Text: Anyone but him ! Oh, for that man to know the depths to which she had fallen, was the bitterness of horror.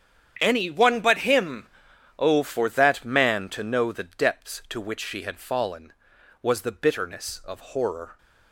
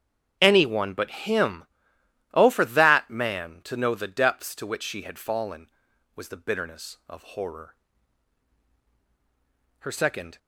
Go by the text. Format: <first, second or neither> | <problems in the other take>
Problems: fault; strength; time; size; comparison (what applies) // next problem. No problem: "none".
first | starts louder than the rest; strong; until 1.4 s; 8 dB; strong in the first // goes on to say "Her second"; from 9.7 s on; 0.58 s long